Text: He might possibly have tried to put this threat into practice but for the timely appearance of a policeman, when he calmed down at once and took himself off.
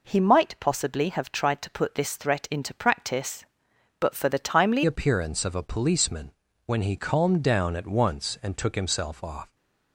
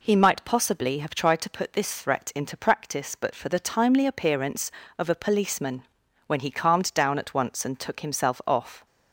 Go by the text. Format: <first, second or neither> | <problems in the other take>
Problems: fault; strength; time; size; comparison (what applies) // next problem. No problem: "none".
second | changes voice at "appearance"; from 4.8 s on; 4.7 s long